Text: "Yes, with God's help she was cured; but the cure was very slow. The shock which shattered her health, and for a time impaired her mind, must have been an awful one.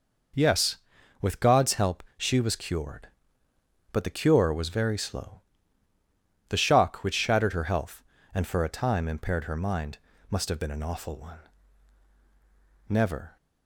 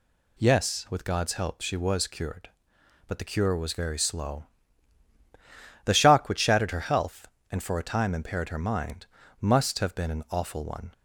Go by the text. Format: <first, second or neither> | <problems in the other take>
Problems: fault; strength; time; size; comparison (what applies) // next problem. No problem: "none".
second | goes on to say "Never"; slight; from 12.8 s on; 0.48 s long